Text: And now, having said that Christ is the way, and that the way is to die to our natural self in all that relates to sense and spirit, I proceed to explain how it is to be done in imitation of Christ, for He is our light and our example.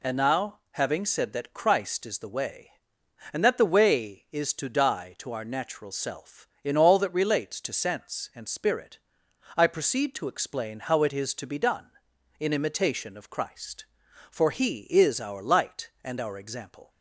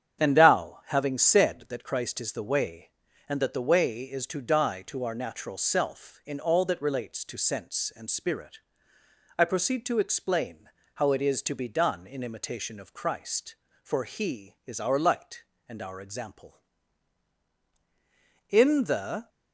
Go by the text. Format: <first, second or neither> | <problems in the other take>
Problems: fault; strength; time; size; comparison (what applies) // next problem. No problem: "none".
first | starts louder than the rest; strong; until 1.2 s; 8 dB // pauses between "explain" and "how"; slight; at 10.6 s; 0.26 s long // goes on to say "In the"; noticeable; from 18.4 s on; 0.80 s long